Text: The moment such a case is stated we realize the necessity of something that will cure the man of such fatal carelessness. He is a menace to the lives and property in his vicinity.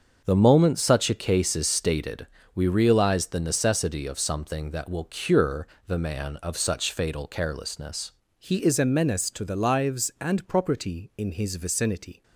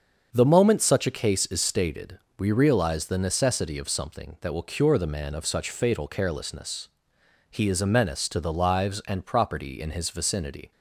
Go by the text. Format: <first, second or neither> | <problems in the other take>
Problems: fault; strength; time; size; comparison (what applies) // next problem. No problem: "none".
second | starts louder than the rest; until 1.2 s; 6.5 dB; also in the second // pauses between "stated" and "we"; slight; at 2.2 s; 0.28 s long; slight in the second // pauses between "cure" and "the"; slight; at 5.6 s; 0.22 s long // changes voice at "He"; from 8.3 s on; 3.9 s long